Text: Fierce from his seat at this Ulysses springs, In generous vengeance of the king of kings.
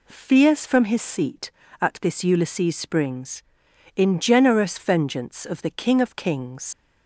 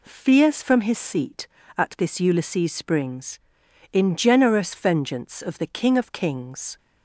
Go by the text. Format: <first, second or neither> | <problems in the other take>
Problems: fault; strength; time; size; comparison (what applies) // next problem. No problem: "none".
second | leaves "kings" unfinished; at 6.7 s; 80 ms